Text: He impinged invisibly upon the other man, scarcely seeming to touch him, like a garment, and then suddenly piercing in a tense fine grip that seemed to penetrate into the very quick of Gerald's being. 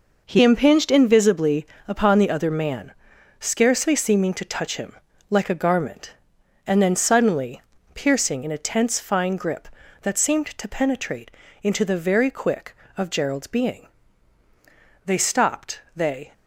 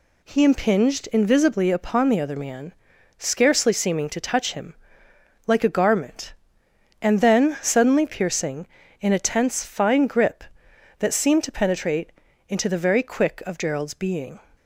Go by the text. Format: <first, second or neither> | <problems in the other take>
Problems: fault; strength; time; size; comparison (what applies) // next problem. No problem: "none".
second | pauses between "invisibly" and "upon"; slight; at 1.6 s; 0.20 s long // pauses between "suddenly" and "piercing"; slight; at 7.6 s; 0.32 s long // pauses between "penetrate" and "into"; slight; at 11.3 s; 0.32 s long; slight in the second // goes on to say "They stopped they"; noticeable; from 15.0 s on; 1.2 s long